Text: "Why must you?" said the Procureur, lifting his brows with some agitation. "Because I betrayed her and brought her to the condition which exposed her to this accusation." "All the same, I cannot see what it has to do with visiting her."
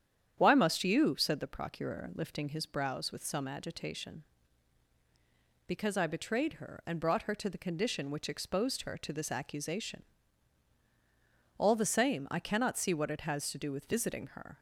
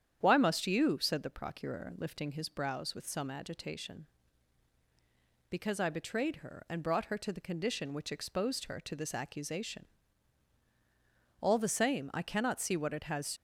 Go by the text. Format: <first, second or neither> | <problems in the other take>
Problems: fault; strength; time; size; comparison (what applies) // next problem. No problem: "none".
first | starts louder than the rest; strong; until 1.2 s; 9 dB; strong in the first // stops before "to do with visiting her"; at 13.3 s